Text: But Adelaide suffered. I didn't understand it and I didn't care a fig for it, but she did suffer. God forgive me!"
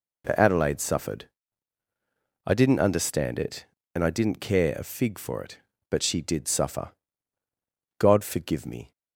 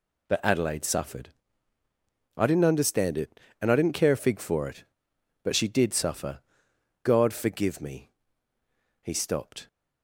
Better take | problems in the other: first | goes on to say "He stopped"; noticeable; from 9.0 s on; 0.64 s long

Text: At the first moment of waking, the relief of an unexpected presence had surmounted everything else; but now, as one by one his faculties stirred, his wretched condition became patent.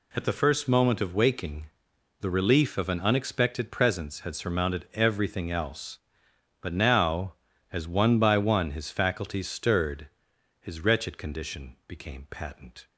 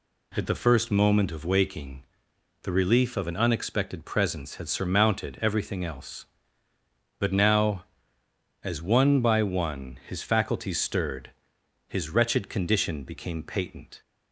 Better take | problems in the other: neither | none

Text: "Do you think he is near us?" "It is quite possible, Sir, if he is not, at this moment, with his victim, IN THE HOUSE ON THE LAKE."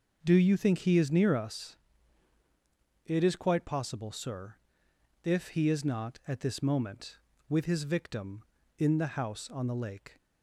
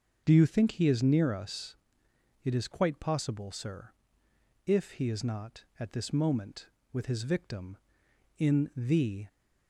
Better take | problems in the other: first | starts louder than the rest; until 1.2 s; 6 dB // stops before "HOUSE ON THE LAKE"; at 9.2 s

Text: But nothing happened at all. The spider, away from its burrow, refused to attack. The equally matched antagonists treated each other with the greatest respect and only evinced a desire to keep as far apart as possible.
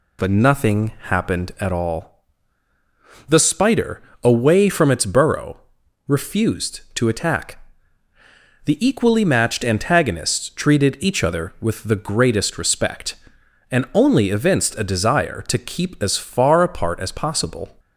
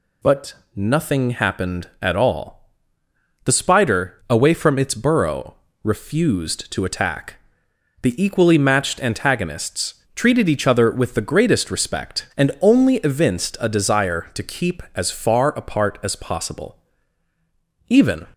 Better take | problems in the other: first | pauses between "But" and "nothing"; slight; at 0.5 s; 0.18 s long // pauses between "antagonists" and "treated"; slight; at 9.9 s; 0.20 s long // goes on to say "Even"; slight; from 17.8 s on; 0.38 s long

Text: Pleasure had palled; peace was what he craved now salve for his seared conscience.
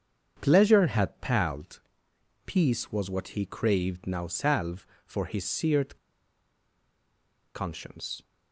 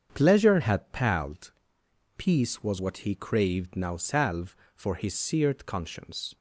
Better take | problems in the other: second | starts louder than the rest; strong; until 1.4 s; 7 dB; strong in the second // pauses between "seared" and "conscience"; strong; at 5.9 s; 1.5 s long

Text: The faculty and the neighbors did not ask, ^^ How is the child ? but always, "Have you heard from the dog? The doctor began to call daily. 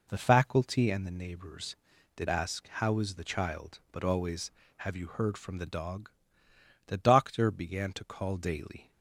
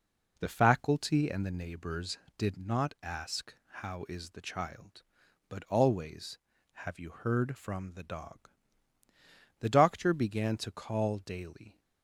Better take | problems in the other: second | skips "not"; at 2.2 s

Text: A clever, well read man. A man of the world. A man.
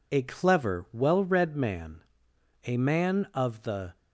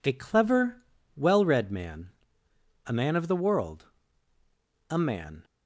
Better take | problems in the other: second | stops before "world A man"; at 3.9 s

